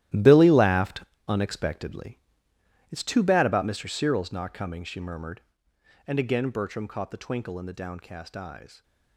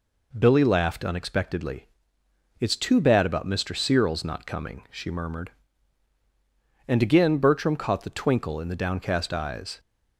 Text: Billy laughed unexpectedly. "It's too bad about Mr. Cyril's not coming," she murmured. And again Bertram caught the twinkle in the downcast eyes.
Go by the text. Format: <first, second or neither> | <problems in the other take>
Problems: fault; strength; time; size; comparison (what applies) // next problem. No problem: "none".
second | gets quieter; strong; throughout; 13.5 dB // pauses between "laughed" and "unexpectedly"; slight; at 1.0 s; 0.22 s long